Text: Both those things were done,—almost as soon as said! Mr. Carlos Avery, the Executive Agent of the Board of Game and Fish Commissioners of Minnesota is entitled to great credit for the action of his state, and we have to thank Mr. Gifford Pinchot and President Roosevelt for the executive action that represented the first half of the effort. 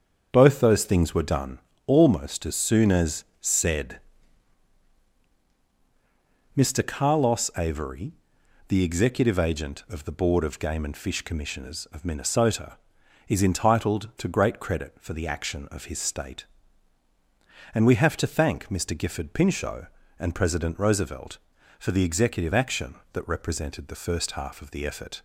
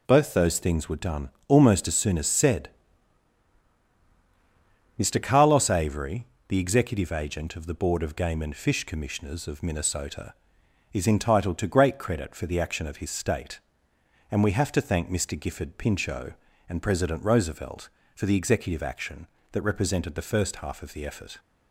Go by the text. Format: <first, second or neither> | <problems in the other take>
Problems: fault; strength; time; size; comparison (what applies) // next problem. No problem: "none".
second | starts louder than the rest; until 1.7 s; 7 dB // pauses between "as" and "said"; slight; at 3.2 s; 0.16 s long